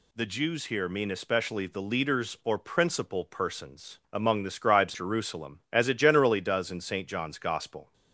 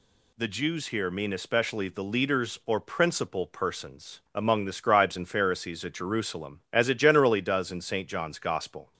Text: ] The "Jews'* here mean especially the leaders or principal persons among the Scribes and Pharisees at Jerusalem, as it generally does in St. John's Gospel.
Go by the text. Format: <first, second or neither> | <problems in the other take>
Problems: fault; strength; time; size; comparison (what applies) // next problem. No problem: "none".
second | skips "and Pharisees at"; at 4.9 s